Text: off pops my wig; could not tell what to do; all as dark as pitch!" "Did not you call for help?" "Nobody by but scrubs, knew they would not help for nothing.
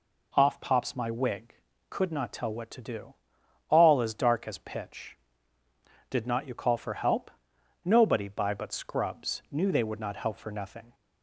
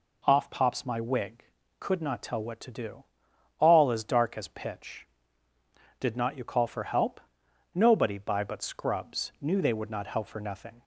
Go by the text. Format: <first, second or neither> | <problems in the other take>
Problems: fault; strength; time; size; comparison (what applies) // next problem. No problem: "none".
neither | none